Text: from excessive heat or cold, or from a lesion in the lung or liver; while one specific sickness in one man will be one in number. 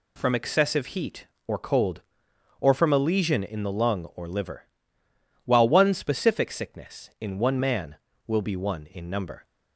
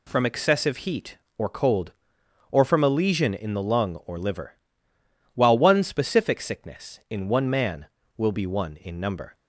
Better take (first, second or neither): neither